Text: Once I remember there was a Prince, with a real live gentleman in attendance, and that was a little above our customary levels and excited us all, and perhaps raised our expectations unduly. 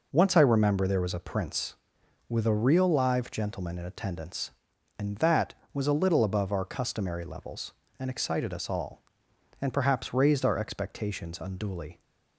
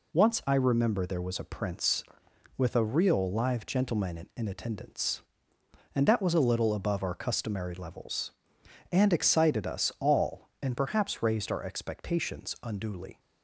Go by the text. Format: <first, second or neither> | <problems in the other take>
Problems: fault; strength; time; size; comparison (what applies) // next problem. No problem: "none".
first | says "in" twice; at 4.3 s